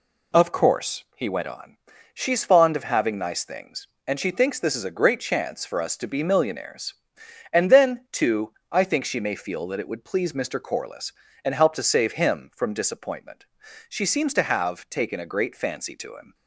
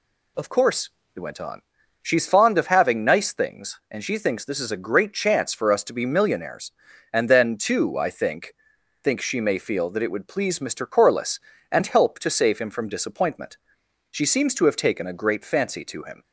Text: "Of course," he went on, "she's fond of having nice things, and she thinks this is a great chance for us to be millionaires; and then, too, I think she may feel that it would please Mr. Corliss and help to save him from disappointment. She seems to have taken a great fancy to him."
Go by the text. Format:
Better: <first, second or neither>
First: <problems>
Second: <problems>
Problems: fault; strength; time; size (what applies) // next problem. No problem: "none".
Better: first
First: none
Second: says "think" twice; at 9.0 s